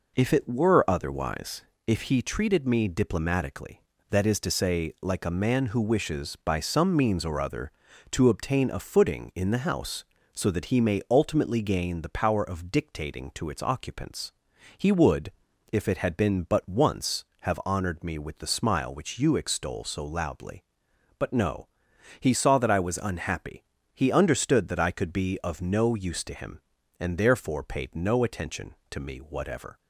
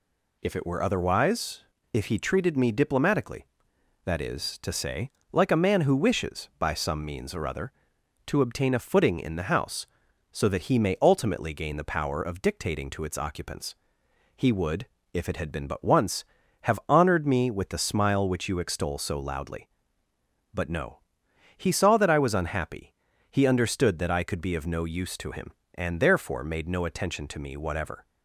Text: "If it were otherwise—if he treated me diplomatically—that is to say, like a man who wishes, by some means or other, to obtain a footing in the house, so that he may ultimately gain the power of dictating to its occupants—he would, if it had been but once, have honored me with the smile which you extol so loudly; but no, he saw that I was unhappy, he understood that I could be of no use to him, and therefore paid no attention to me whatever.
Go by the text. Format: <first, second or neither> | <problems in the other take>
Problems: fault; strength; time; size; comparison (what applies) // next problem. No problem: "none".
first | says "made" for "paid"; at 26.4 s